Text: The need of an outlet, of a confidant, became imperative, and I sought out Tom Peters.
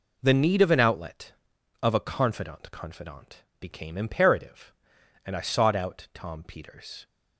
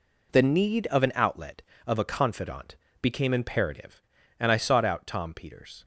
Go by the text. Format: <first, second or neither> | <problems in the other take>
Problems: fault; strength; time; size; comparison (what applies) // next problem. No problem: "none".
second | says "confidant" twice; at 2.7 s